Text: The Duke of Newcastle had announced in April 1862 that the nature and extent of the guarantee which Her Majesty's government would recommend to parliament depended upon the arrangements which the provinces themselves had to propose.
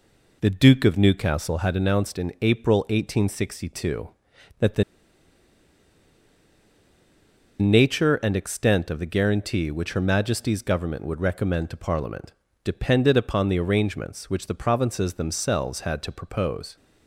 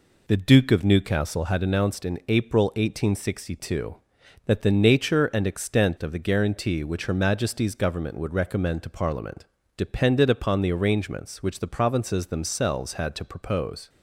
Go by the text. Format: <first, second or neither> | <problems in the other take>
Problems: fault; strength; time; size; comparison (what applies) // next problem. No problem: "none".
second | pauses between "the" and "nature"; strong; at 4.8 s; 2.7 s long // pauses between "parliament" and "depended"; slight; at 12.3 s; 0.30 s long; slight in the second